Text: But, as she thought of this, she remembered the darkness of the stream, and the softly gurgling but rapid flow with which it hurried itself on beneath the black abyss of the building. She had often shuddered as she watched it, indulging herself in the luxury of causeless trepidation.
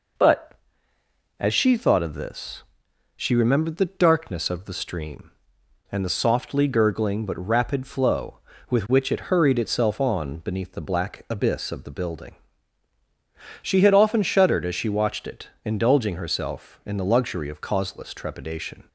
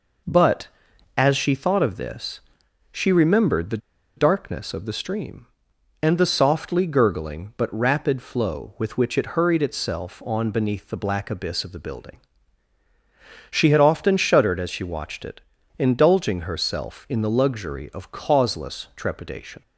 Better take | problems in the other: first | pauses between "the" and "darkness"; at 3.7 s; 0.39 s long

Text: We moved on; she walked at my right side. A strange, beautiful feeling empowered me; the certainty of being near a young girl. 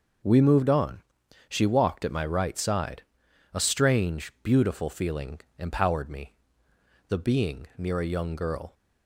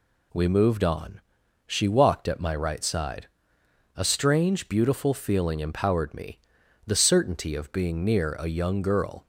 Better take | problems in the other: second | pauses between "feeling" and "empowered"; slight; at 5.4 s; 0.16 s long // skips "certainty of"; at 7.1 s

